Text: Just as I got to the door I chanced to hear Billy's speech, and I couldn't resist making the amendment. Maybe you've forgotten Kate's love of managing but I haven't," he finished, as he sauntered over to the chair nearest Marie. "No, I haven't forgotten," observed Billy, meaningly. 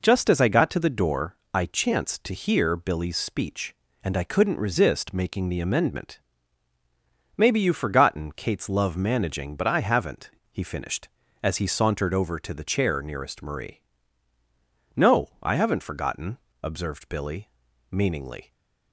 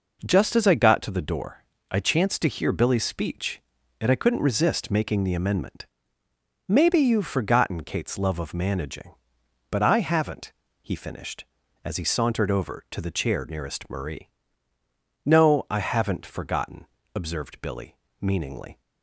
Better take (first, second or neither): second